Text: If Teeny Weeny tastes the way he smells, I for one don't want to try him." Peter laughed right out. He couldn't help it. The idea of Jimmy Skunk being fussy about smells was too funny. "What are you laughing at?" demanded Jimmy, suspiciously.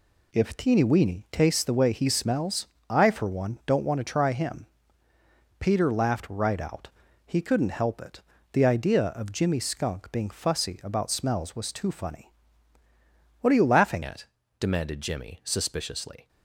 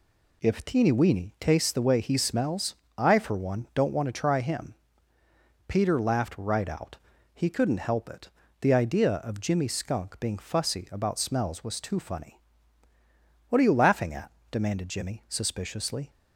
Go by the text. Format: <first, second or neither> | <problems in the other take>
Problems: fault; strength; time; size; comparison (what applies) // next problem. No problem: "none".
second | changes voice at "at"; from 14.0 s on; 2.2 s long